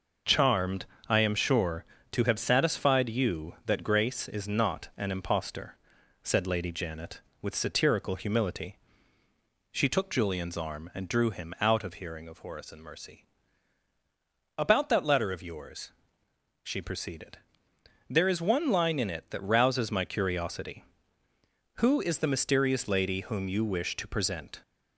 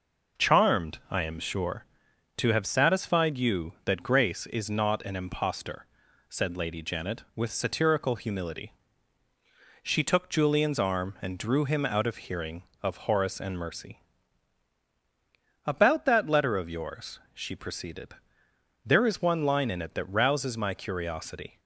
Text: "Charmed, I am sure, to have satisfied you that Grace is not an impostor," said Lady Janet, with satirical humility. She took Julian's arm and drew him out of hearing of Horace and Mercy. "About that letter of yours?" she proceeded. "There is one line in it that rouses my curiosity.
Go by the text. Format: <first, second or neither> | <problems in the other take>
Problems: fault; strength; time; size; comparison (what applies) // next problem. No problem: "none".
second | goes on to say "Who is the mysterious lady whom you wish to present"; strong; from 21.7 s on; 2.8 s long